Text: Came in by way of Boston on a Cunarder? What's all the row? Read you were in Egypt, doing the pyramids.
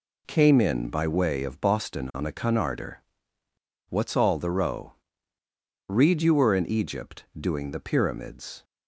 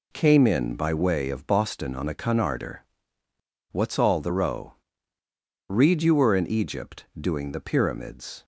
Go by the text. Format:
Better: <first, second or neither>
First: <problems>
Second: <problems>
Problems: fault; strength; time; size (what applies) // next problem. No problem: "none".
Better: neither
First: none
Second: none